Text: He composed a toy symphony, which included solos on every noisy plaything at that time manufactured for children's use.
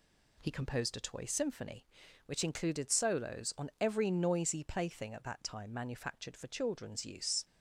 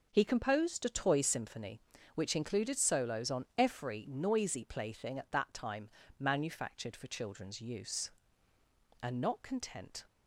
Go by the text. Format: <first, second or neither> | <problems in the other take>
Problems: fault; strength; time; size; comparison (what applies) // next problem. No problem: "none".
first | pauses between "time" and "manufactured"; slight; at 5.8 s; 0.30 s long // goes on to say "And not content"; noticeable; from 9.0 s on; 1.0 s long